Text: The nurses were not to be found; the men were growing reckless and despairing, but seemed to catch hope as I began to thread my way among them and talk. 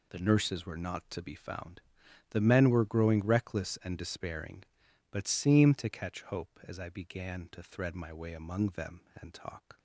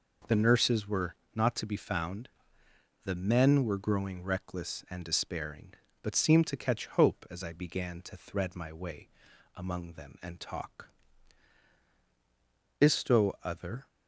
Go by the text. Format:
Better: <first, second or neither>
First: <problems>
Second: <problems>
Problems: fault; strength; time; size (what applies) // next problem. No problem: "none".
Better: first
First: none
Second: pauses between "were" and "not"; slight; at 1.1 s; 0.20 s long // pauses between "way" and "among"; noticeable; at 9.0 s; 0.46 s long // goes on to say "ISTo other"; noticeable; from 12.8 s on; 1.0 s long